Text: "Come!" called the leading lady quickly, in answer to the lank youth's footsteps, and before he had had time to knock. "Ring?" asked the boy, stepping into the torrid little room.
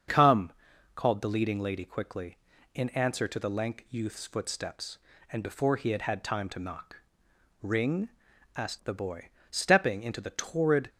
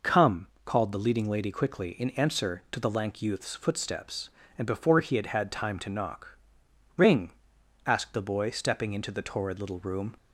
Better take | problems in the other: second | starts louder than the rest; strong; until 1.5 s; 7 dB // stops before "little room"; at 10.8 s

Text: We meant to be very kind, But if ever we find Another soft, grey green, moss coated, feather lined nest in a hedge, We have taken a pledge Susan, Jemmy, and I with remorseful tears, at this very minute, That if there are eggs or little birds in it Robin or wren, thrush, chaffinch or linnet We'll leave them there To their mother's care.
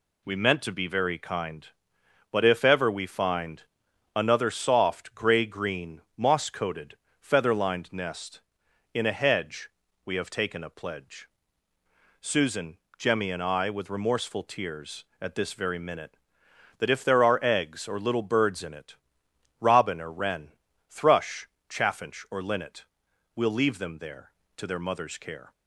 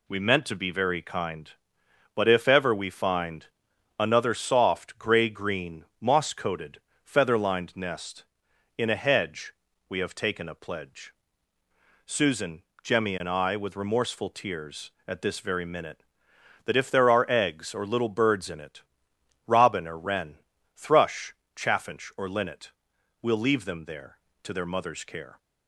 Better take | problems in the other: neither | pauses between "find" and "Another"; noticeable; the same in both // pauses between "pledge" and "Susan"; noticeable; the same in both // pauses between "it" and "Robin"; noticeable; the same in both // pauses between "linnet" and "We'll"; noticeable; the same in both

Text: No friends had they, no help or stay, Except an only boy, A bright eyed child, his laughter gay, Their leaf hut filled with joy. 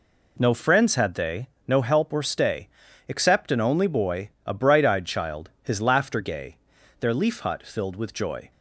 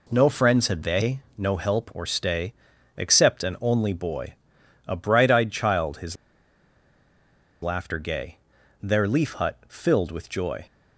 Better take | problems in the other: first | pauses between "his" and "laughter"; strong; at 6.1 s; 1.4 s long

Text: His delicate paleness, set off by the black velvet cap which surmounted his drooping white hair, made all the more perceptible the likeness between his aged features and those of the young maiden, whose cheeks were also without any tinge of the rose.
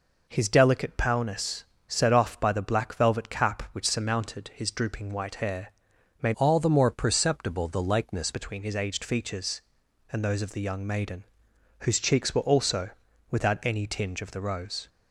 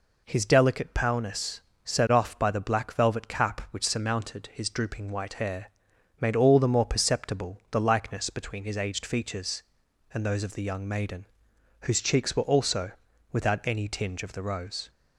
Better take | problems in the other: second | changes voice from "all" to "likeness"; from 6.3 to 8.3 s; 2.0 s long // pauses between "also" and "without"; at 12.9 s; 0.40 s long; also in the second

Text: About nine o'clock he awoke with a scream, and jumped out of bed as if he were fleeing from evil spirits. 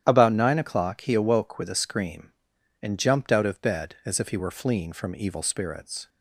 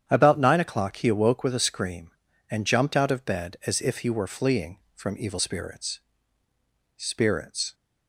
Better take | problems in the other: first | starts louder than the rest; strong; until 1.0 s; 9 dB; strong in the first // says "spirits" twice; at 6.9 s

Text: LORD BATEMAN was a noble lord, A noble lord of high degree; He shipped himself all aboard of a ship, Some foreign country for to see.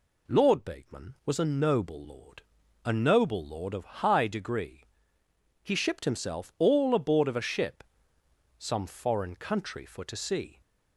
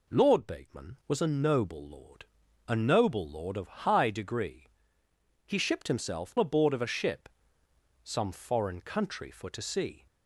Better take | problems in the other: first | skips "all"; at 6.3 s

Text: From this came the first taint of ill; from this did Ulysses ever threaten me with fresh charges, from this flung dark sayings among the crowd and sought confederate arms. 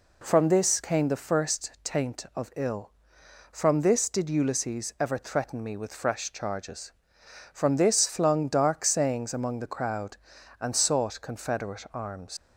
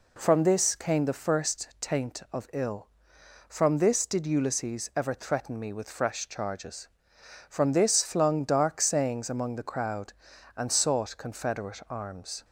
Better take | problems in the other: second | leaves "arms" unfinished; at 12.3 s; 110 ms

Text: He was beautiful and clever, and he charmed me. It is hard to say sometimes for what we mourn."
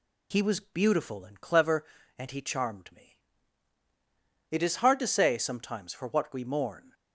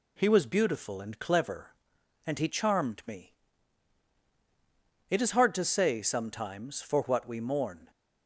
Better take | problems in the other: neither | none

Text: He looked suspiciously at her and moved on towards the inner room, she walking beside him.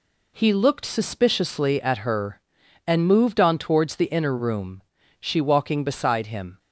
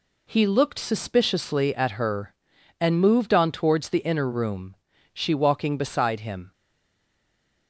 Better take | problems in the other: first | stays silent after the last word; noticeable; from 6.5 s on; 1.1 s long

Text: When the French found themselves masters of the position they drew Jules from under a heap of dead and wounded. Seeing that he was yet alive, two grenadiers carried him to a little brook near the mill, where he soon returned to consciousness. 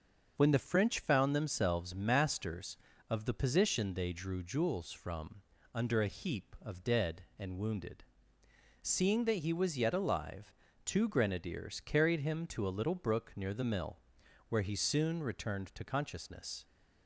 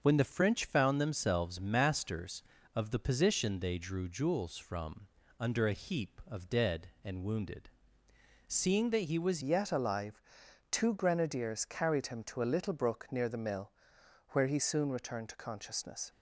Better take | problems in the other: first | starts louder than the rest; until 1.0 s; 6.5 dB; also in the first // pauses between "from" and "under"; slight; at 5.0 s; 0.32 s long; slight in the first // changes voice at "yet"; from 9.4 s on; 6.6 s long

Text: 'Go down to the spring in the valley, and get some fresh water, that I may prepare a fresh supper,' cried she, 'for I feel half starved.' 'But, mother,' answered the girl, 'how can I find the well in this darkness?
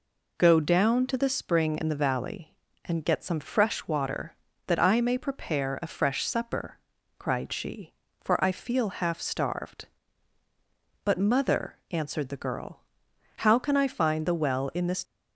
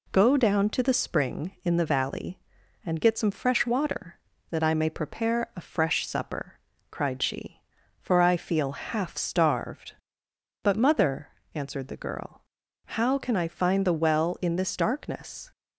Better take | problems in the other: second | stops before "darkness"; at 15.0 s

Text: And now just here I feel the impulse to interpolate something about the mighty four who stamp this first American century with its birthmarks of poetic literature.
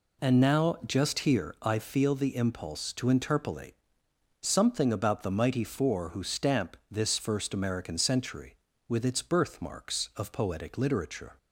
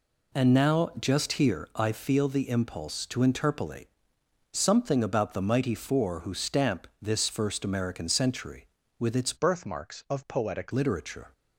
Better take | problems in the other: first | pauses between "interpolate" and "something"; noticeable; at 3.8 s; 0.66 s long; noticeable in the first // changes voice from "birthmarks" to "poetic"; from 9.3 to 10.7 s; 1.4 s long

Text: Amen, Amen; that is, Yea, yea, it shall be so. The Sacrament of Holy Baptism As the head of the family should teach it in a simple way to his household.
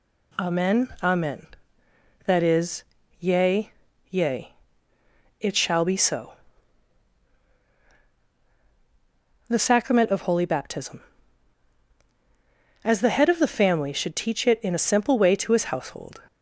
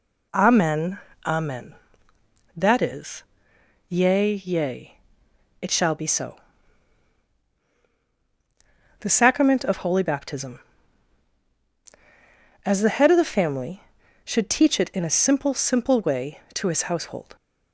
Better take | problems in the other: first | says "simple" twice; at 15.5 s

